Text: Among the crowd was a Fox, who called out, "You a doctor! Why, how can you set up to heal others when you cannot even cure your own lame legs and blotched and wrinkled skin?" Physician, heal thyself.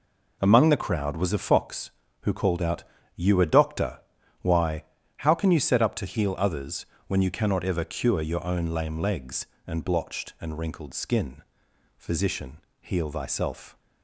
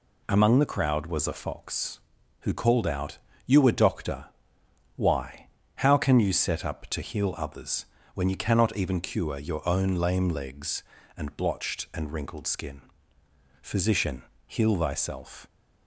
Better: second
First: pauses between "others" and "when"; slight; at 6.8 s; 0.24 s long // says "ever" for "even"; at 7.6 s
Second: pauses between "others" and "when"; slight; at 7.8 s; 0.30 s long

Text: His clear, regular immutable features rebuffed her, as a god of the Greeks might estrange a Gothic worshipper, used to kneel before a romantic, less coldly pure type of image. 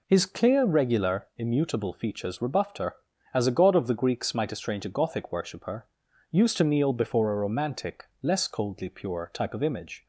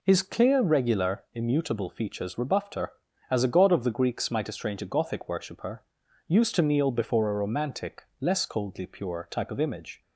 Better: neither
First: none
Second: none

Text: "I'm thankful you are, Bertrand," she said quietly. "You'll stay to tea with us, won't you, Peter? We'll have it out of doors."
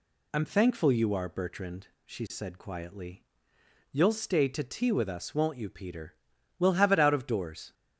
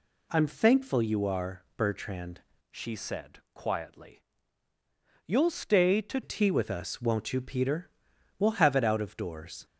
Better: first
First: none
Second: changes voice from "she" to "to"; from 2.7 to 6.2 s; 3.5 s long

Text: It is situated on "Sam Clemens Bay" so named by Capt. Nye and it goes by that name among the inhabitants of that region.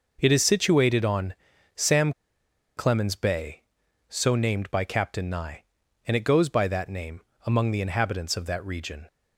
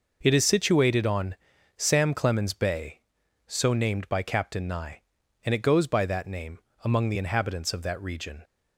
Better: second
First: pauses between "on" and "Sam"; at 1.3 s; 0.42 s long // pauses between "Sam" and "Clemens"; noticeable; at 2.1 s; 0.65 s long // pauses between "name" and "among"; slight; at 7.2 s; 0.24 s long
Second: pauses between "on" and "Sam"; at 1.3 s; 0.42 s long // pauses between "name" and "among"; slight; at 6.5 s; 0.24 s long

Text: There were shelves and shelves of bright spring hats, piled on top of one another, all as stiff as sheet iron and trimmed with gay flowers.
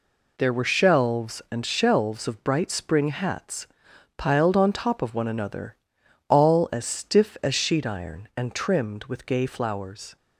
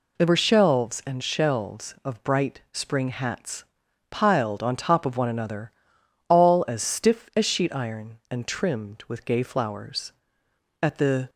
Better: first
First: none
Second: goes on to say "At the"; slight; from 10.8 s on; 0.48 s long

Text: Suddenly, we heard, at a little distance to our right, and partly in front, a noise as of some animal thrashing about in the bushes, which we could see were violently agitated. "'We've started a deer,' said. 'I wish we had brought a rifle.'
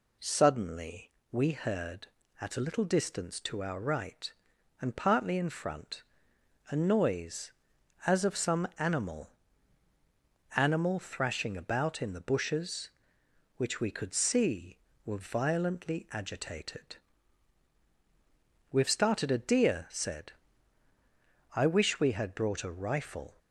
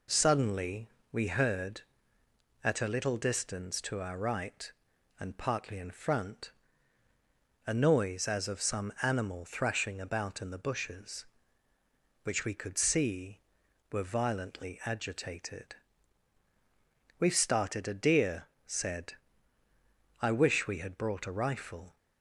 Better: second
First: says "animal" twice; at 10.5 s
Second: none

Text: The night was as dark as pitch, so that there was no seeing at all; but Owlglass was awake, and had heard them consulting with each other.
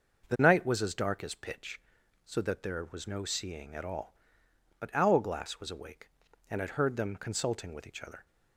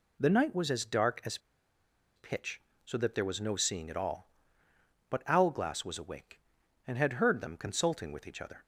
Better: first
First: none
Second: pauses between "as" and "pitch"; noticeable; at 1.3 s; 0.78 s long

